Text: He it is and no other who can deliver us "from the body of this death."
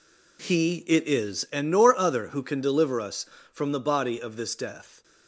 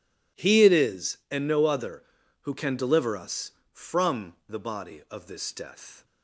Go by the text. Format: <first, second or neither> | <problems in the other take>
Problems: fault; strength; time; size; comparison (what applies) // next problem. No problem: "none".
second | says "nor" for "no"; at 1.7 s